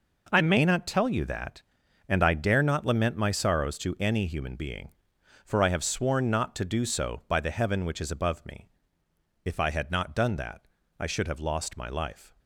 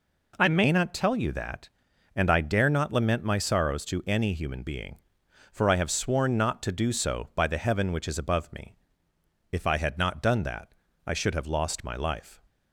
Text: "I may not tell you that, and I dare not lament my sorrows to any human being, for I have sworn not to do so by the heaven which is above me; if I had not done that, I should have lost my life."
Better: second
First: gets quieter; strong; throughout; 11.5 dB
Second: none

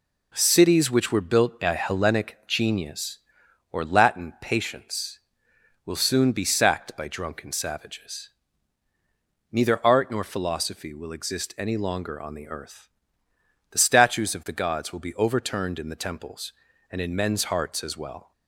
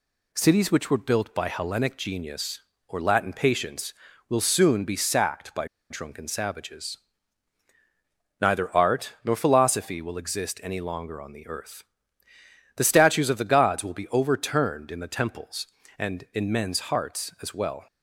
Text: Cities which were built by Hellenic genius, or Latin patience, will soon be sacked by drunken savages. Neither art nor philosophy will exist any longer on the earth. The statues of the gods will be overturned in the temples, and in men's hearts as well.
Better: first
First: none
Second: pauses between "by" and "drunken"; slight; at 5.6 s; 0.24 s long

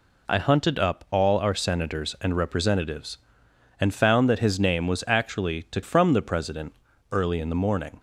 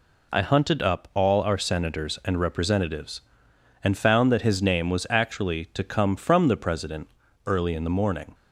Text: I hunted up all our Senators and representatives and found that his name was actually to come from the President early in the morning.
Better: second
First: skips "come"; at 5.8 s // pauses between "President" and "early"; at 6.7 s; 0.38 s long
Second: pauses between "President" and "early"; at 7.0 s; 0.38 s long

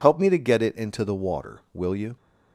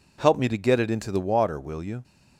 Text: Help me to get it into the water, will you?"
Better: neither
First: none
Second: none

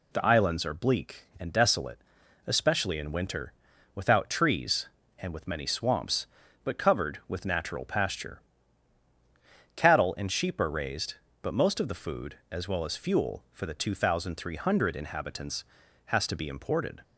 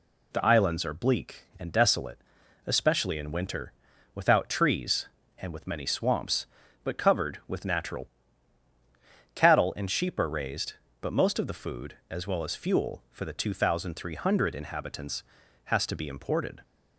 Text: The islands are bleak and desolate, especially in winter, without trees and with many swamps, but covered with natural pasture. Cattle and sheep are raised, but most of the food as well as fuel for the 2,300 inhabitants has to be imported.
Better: first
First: none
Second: skips "pasture"; at 8.6 s

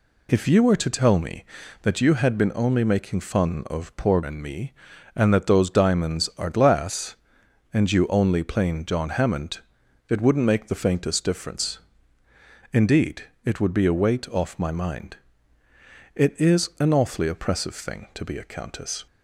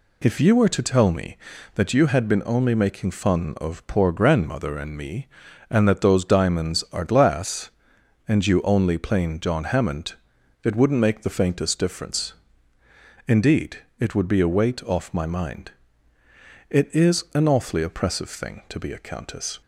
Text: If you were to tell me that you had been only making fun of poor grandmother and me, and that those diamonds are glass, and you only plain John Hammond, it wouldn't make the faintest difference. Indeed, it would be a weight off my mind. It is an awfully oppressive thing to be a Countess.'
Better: second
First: skips "grandmother"; at 4.2 s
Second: none

